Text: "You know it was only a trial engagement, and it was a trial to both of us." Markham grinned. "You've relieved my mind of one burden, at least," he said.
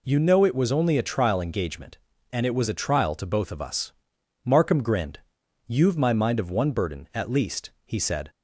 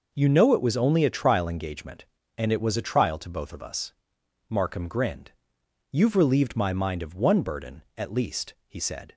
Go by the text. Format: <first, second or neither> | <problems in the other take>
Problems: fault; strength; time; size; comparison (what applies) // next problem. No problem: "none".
second | skips "relieved"; at 5.9 s